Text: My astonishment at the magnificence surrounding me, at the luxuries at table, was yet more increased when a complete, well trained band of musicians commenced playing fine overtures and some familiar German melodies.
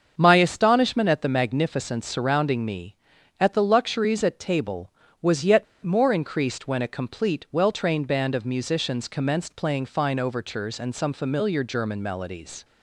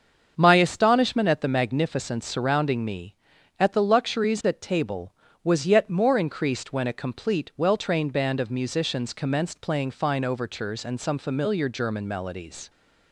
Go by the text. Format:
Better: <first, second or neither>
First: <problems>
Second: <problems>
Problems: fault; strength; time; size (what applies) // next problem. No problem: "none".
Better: second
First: starts louder than the rest; until 1.1 s; 7 dB // pauses between "yet" and "more"; slight; at 5.6 s; 0.17 s long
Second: starts louder than the rest; until 1.3 s; 7 dB